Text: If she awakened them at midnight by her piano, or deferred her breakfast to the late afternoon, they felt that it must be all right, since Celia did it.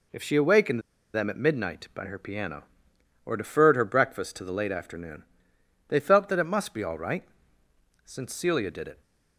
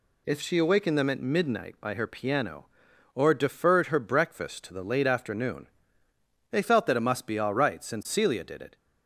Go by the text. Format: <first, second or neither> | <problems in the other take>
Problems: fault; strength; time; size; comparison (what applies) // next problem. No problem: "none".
second | pauses between "awakened" and "them"; slight; at 0.8 s; 0.33 s long